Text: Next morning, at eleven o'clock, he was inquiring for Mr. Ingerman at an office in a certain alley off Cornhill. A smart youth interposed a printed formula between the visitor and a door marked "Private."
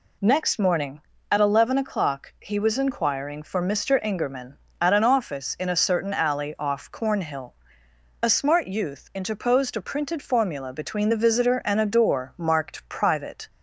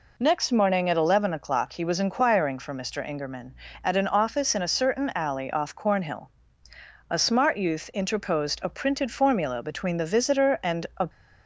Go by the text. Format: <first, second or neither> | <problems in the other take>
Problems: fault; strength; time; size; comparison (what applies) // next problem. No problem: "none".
first | stops before "door marked Private"; at 11.0 s